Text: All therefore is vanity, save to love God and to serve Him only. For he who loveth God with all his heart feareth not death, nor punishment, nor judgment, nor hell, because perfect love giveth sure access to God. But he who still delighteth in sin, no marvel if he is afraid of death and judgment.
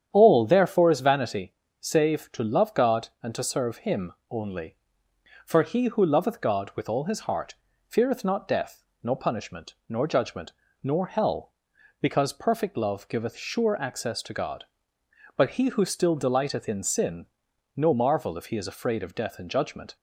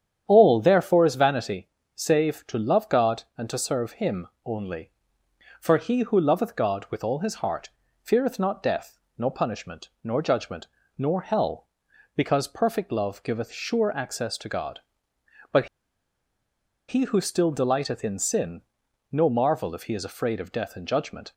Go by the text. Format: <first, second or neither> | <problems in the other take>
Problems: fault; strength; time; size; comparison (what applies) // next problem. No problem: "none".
first | starts louder than the rest; strong; until 1.2 s; 9 dB; strong in the first // pauses between "Him" and "only"; slight; at 4.2 s; 0.18 s long; slight in the first // pauses between "heart" and "feareth"; slight; at 7.7 s; 0.32 s long; slight in the first // pauses between "But" and "he"; at 15.6 s; 1.2 s long